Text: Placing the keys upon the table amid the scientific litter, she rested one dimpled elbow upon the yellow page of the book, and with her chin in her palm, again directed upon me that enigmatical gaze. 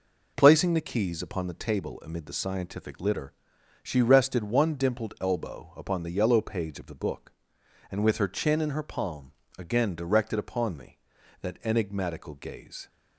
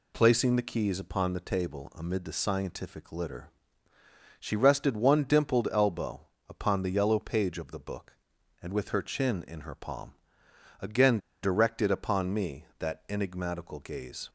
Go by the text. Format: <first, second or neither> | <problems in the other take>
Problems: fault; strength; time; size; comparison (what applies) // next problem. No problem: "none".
first | pauses between "elbow" and "upon"; slight; at 6.2 s; 0.22 s long // pauses between "again" and "directed"; slight; at 11.1 s; 0.23 s long